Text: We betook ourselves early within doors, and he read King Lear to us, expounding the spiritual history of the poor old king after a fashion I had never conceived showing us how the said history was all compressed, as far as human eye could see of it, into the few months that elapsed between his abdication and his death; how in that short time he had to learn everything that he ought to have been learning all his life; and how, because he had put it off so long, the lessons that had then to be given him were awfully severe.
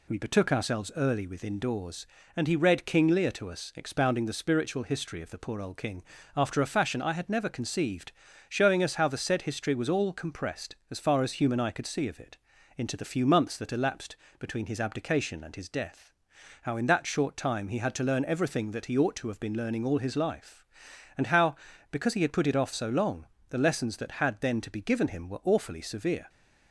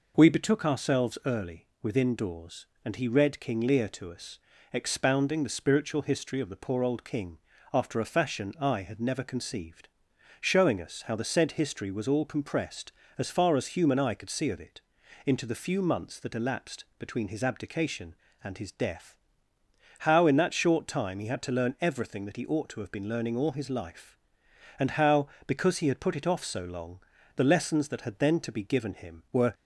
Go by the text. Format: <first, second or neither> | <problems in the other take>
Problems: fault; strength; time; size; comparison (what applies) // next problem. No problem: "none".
first | pauses between "early" and "within"; slight; at 1.6 s; 0.16 s long // pauses between "king" and "after"; slight; at 7.3 s; 0.36 s long; slight in the first // pauses between "conceived" and "showing"; noticeable; at 9.8 s; 0.54 s long; also in the first // pauses between "elapsed" and "between"; slight; at 16.8 s; 0.16 s long; slight in the first // stops before "awfully severe"; at 29.5 s